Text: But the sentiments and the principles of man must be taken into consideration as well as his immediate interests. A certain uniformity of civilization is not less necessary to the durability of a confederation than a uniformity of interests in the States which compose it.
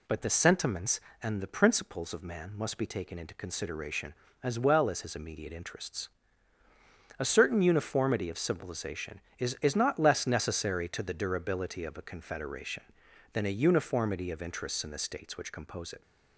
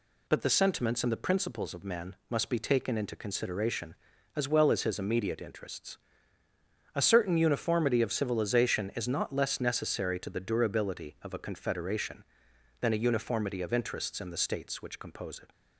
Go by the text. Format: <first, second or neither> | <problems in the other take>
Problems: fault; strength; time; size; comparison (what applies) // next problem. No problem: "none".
second | says "is" twice; at 9.6 s